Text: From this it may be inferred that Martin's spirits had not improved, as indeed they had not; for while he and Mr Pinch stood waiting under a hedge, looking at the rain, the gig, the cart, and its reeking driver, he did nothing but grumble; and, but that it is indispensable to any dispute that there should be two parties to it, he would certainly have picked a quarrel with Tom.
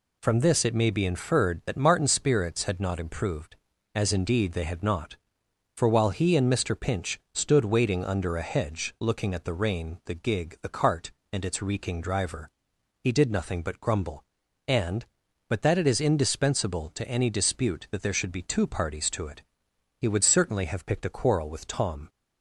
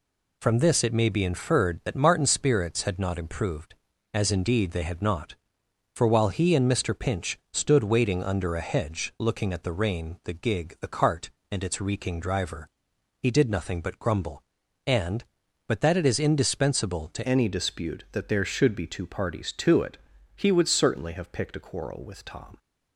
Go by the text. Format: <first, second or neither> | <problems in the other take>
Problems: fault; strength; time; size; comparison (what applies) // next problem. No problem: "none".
first | changes voice at "any"; from 17.2 s on; 5.3 s long